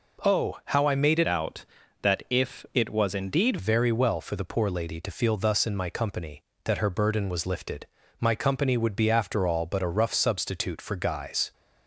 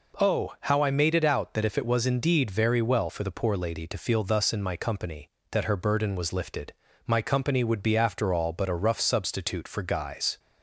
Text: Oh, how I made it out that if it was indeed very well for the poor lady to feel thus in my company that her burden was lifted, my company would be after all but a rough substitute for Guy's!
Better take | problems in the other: second | changes voice from "out" to "indeed"; from 1.2 to 3.5 s; 2.3 s long

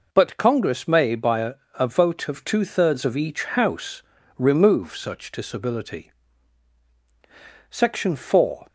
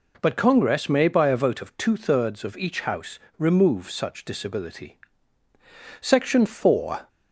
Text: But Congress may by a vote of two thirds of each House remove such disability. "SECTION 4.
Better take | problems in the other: second | says "a" twice; at 1.7 s // pauses between "House" and "remove"; slight; at 4.0 s; 0.34 s long; slight in the second

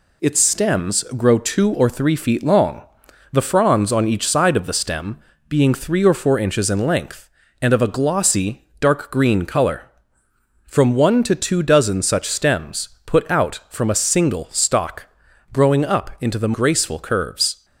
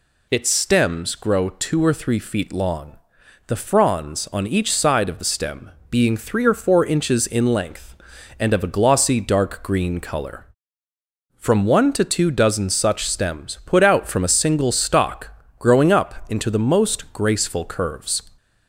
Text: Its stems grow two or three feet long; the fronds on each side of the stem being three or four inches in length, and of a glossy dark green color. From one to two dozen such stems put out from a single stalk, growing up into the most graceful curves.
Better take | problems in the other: second | pauses between "stem" and "being"; slight; at 5.1 s; 0.32 s long; slight in the second // pauses between "stems" and "put"; slight; at 12.8 s; 0.18 s long // skips "most"; at 16.5 s

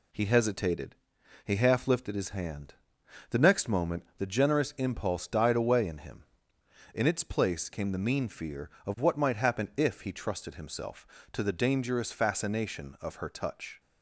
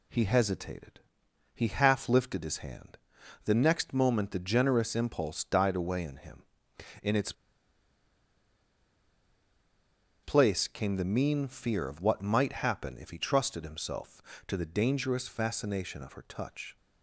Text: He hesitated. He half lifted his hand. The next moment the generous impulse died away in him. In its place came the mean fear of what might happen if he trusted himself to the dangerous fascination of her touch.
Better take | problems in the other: first | pauses between "its" and "place"; strong; at 7.3 s; 2.9 s long

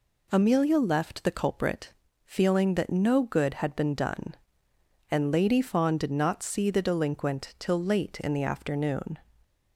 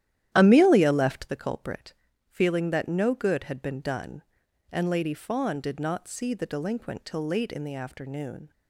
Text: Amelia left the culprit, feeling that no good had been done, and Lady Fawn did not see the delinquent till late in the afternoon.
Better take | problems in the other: first | starts louder than the rest; strong; until 1.3 s; 12 dB

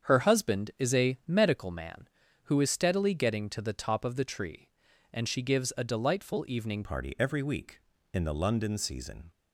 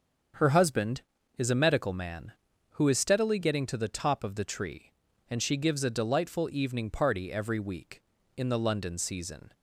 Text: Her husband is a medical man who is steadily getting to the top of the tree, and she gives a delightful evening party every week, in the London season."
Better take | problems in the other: second | starts louder than the rest; strong; until 1.1 s; 7.5 dB; strong in the second // changes voice at "party"; from 6.8 s on; 2.5 s long

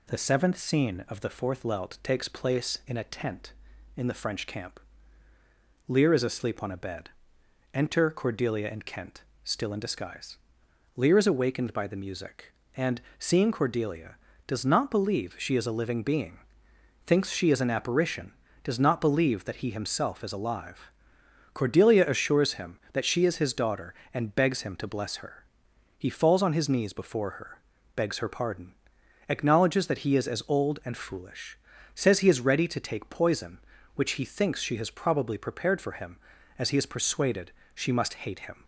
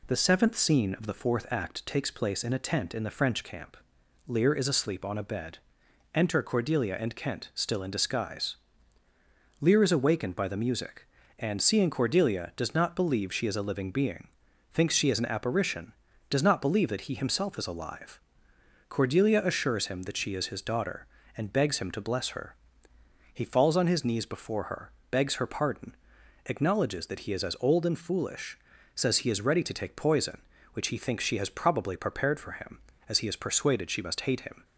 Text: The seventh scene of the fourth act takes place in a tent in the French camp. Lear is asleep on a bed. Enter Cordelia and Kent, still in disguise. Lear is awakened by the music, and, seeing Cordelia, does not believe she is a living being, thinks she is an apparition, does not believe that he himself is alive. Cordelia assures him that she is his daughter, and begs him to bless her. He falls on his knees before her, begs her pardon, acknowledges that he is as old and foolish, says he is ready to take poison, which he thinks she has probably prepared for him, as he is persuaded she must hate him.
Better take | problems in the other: second | says "lelt" for "act"; at 1.6 s // pauses between "persuaded" and "she"; slight; at 37.5 s; 0.24 s long

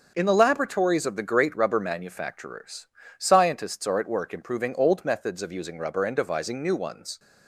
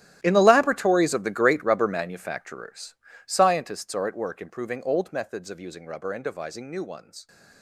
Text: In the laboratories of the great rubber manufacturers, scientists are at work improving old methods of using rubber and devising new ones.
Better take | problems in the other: first | gets quieter; strong; throughout; 18 dB // starts louder than the rest; strong; until 1.2 s; 13.5 dB; also in the first

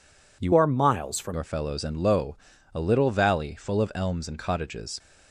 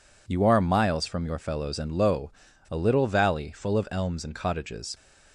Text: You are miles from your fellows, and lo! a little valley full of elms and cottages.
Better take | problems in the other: second | changes voice from "are" to "from"; from 0.5 to 1.3 s; 0.8 s long

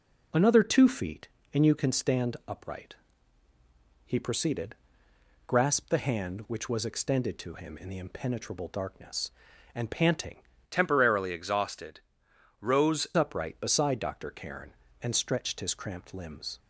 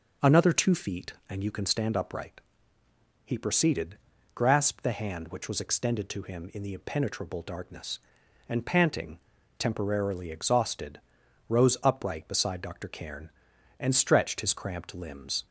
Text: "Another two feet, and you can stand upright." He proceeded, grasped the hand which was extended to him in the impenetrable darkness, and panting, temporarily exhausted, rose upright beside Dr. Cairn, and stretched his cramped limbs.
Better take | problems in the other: second | changes voice from "temporarily" to "rose"; from 10.6 to 13.0 s; 2.4 s long

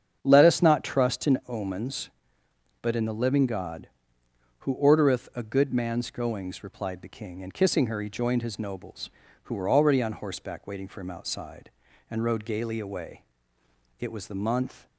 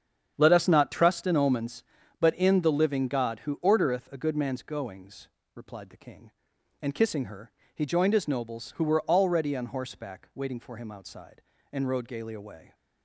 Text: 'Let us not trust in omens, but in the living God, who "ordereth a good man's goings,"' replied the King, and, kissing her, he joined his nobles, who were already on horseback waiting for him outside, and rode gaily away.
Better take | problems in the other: second | starts louder than the rest; strong; until 1.2 s; 7.5 dB; strong in the second // goes on to say "It was the month"; noticeable; from 13.9 s on; 0.88 s long

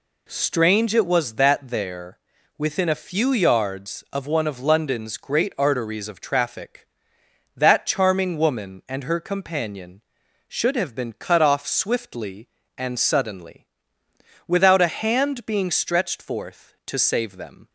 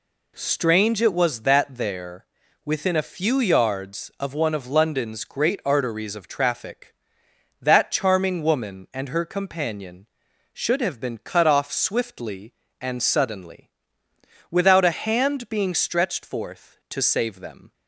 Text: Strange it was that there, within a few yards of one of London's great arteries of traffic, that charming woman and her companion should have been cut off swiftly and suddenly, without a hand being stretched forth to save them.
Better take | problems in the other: neither | none

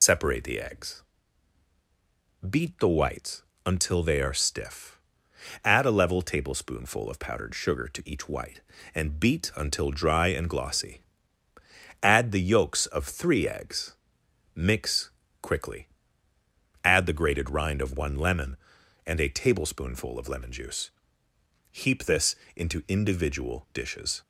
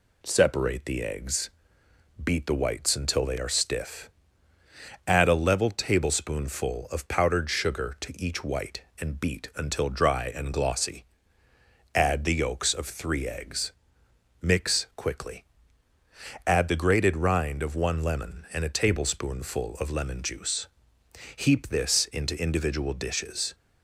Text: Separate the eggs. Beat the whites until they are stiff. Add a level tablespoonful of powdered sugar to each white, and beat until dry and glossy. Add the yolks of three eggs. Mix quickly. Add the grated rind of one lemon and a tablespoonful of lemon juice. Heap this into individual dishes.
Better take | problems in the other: second | loses the start of "Separate"; at 0.0 s; 105 ms // pauses between "whites" and "until"; slight; at 3.4 s; 0.22 s long // pauses between "Mix" and "quickly"; slight; at 15.0 s; 0.32 s long // pauses between "this" and "into"; slight; at 22.3 s; 0.20 s long

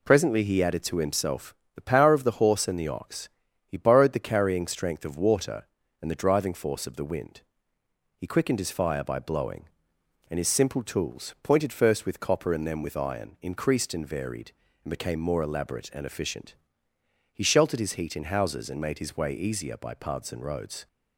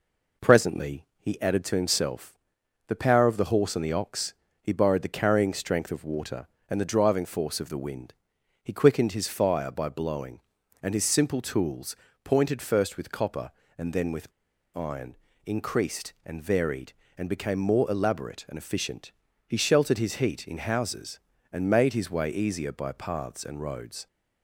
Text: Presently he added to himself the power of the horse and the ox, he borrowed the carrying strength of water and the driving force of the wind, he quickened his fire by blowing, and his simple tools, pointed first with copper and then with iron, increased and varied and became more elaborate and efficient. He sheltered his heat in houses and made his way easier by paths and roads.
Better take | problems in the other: first | pauses between "himself" and "the"; noticeable; at 2.3 s; 0.50 s long; slight in the first // pauses between "with" and "iron"; at 14.3 s; 0.43 s long

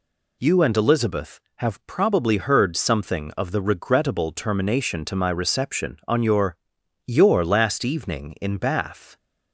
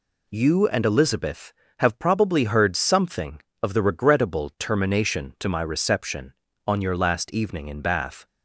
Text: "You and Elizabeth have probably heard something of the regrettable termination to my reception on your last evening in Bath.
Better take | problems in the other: second | says "your" twice; at 7.0 s

